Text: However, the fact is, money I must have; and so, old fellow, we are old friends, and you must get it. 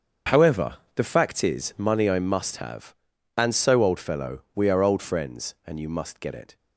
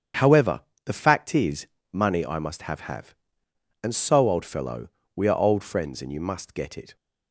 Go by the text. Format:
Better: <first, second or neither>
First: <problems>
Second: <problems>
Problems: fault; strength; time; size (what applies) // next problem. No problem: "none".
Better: first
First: starts louder than the rest; strong; until 1.4 s; 7 dB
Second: starts louder than the rest; strong; until 1.4 s; 8 dB // says "have" twice; at 2.9 s